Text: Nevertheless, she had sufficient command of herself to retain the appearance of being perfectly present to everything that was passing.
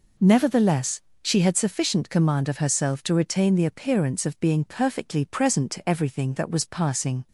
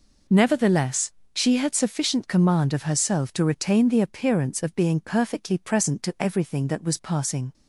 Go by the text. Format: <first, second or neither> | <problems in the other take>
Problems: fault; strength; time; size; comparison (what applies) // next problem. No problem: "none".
neither | none